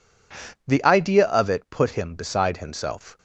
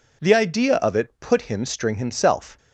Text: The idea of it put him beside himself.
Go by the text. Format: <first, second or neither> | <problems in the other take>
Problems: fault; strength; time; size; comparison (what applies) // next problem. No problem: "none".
first | says "string" for "beside"; at 1.6 s